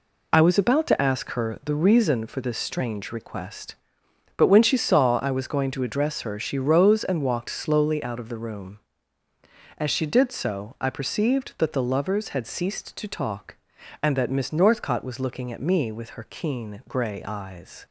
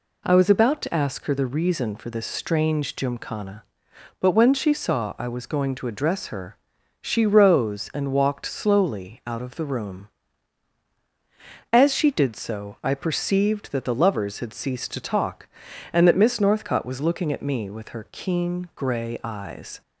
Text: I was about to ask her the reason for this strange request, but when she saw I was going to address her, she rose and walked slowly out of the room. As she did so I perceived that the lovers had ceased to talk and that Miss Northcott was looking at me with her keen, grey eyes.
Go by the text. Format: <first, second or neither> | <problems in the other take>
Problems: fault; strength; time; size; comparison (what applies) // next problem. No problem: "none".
first | says "gymkhana" for "request"; at 2.9 s